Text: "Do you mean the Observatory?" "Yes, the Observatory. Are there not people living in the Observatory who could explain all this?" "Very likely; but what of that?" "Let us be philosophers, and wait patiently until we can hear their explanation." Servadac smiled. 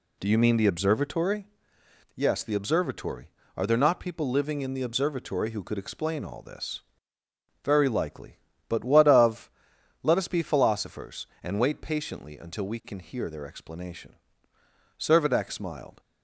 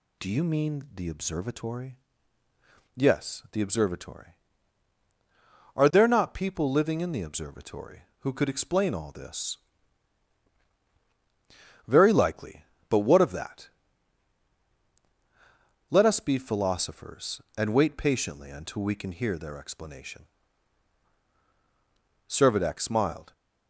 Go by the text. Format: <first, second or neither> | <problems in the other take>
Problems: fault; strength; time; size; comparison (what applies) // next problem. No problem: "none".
second | skips "that"; at 9.7 s